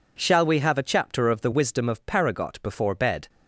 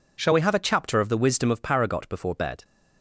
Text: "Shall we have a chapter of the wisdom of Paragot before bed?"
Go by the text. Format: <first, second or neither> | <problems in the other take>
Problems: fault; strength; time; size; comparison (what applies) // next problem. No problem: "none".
neither | none